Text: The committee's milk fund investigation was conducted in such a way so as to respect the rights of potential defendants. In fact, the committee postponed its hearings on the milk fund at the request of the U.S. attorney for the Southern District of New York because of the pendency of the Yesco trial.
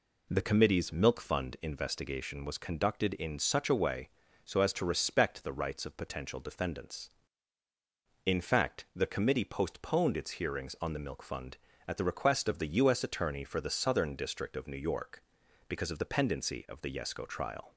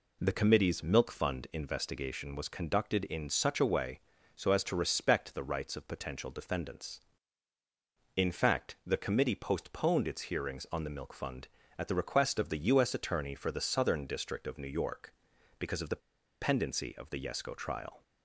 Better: first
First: none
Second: pauses between "the" and "pendency"; at 16.0 s; 0.41 s long

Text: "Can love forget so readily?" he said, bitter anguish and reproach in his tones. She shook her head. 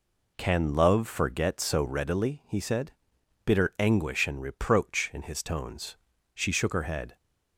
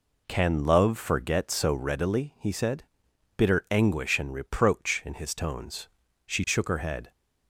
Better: neither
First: none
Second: none

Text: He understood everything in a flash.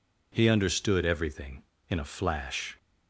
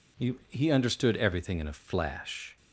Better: first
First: none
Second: says "He" twice; at 0.4 s

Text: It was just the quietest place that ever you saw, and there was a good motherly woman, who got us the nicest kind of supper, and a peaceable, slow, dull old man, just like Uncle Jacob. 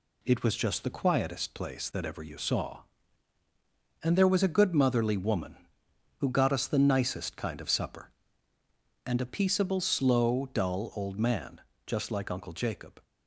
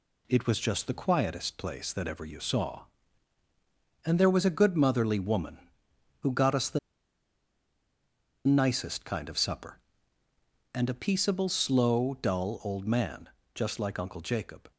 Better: first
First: none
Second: pauses between "the" and "nicest"; strong; at 6.7 s; 1.6 s long

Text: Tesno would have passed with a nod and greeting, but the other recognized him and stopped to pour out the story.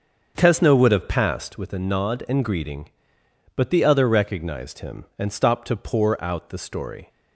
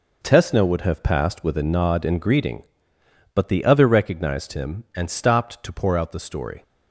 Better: second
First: starts louder than the rest; until 1.7 s; 6.5 dB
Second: none

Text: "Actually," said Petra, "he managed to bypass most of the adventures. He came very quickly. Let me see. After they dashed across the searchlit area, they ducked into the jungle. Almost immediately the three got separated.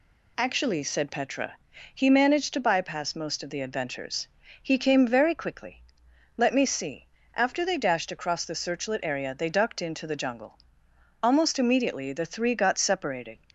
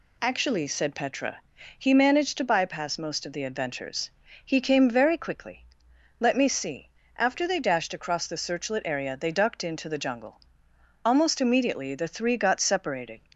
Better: neither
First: none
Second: none

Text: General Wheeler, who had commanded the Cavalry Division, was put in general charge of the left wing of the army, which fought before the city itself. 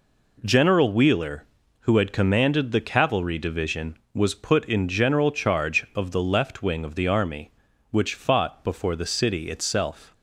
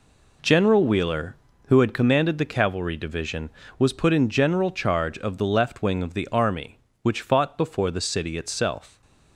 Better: neither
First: none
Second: none

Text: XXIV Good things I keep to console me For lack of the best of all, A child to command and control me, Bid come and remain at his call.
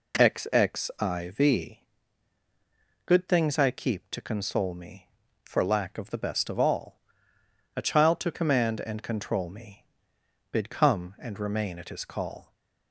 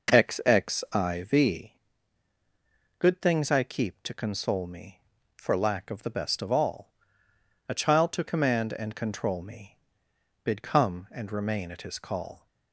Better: first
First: pauses between "XXIV" and "Good"; at 1.7 s; 1.2 s long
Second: starts louder than the rest; noticeable; until 1.5 s; 5.5 dB // pauses between "XXIV" and "Good"; at 1.7 s; 1.2 s long

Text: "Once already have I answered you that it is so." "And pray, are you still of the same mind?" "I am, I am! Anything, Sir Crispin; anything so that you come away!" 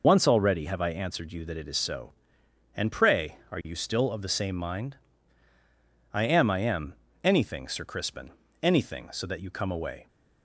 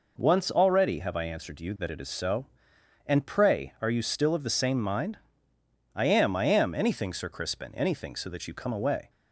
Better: second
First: loses the start of "Once"; at 0.0 s; 50 ms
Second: none

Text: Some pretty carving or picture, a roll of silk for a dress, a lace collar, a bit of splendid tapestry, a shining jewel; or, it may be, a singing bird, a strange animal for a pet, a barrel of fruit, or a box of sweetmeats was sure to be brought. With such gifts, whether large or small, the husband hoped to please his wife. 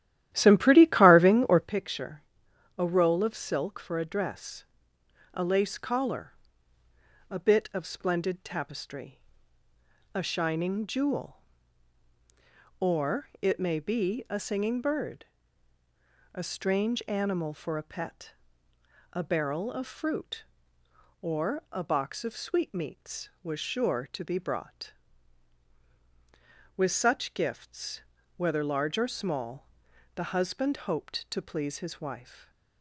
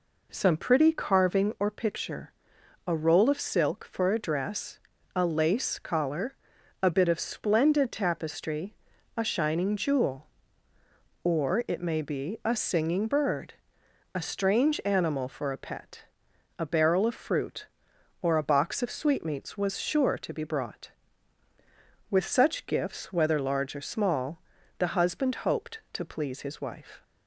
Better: second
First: starts louder than the rest; strong; until 1.8 s; 12.5 dB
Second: none

